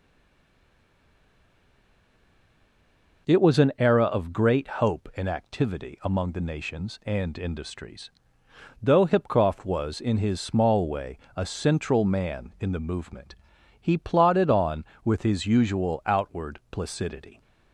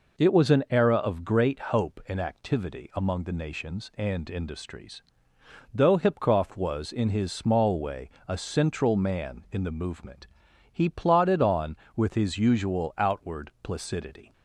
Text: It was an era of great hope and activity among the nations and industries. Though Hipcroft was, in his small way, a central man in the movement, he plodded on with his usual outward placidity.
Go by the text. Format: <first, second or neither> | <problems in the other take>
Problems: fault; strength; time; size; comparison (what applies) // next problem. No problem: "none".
second | stays silent before the first word; strong; until 3.2 s; 3.2 s long